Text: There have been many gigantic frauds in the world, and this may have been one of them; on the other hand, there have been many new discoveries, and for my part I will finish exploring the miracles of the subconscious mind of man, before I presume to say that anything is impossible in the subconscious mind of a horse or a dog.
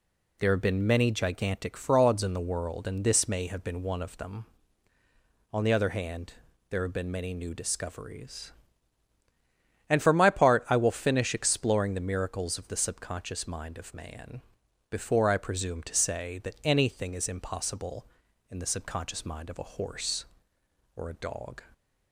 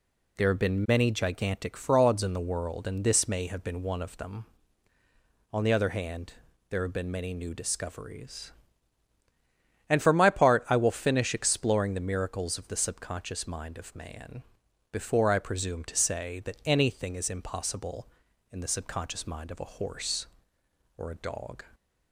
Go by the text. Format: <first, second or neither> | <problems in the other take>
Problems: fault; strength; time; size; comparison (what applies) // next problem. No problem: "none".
neither | none